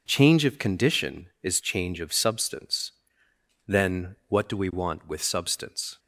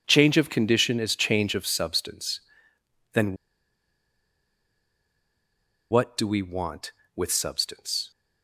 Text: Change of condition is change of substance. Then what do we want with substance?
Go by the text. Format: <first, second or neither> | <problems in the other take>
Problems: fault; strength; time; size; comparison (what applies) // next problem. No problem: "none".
first | pauses between "Then" and "what"; strong; at 3.3 s; 2.5 s long